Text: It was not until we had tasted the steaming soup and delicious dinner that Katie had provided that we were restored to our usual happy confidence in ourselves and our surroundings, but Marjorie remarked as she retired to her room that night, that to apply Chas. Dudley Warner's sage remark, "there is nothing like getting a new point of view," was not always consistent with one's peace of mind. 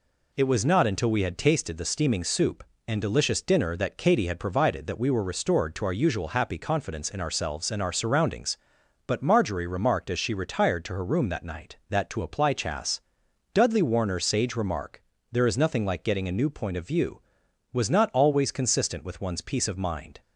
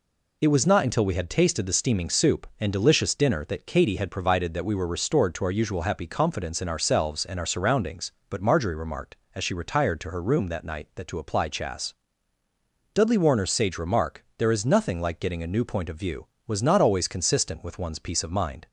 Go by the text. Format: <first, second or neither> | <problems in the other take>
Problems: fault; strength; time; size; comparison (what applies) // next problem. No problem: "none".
neither | none